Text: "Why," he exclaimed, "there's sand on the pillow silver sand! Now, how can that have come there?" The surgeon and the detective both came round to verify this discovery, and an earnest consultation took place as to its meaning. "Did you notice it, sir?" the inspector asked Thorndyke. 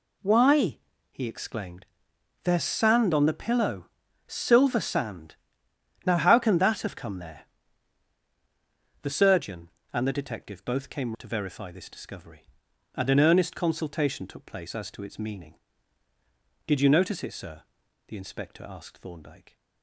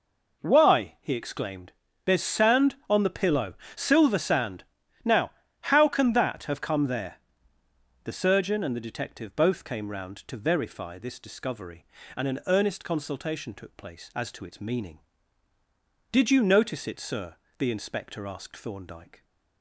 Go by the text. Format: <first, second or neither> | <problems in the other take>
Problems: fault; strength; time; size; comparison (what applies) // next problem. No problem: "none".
second | pauses between "pillow" and "silver"; at 3.8 s; 0.40 s long; slight in the second // skips "round"; at 11.1 s